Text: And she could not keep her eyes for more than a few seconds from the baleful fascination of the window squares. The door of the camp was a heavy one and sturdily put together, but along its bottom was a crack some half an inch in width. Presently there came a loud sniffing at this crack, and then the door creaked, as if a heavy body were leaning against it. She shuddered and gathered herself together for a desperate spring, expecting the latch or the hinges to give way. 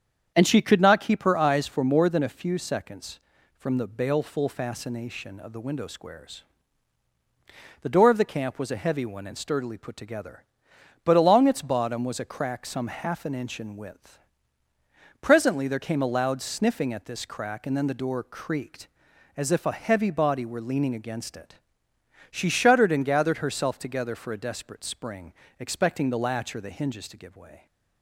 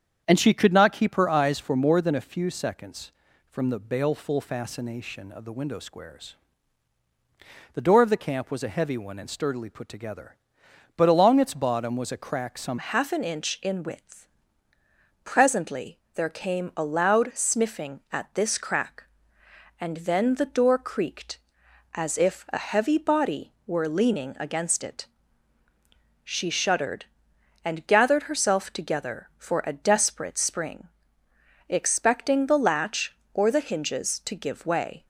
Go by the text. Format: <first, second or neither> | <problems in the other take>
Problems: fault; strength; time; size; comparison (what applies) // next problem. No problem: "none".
first | starts louder than the rest; strong; until 1.2 s; 8 dB; strong in the first // changes voice at "half"; from 12.7 s on; 22.3 s long // pauses between "Presently" and "there"; slight; at 15.9 s; 0.16 s long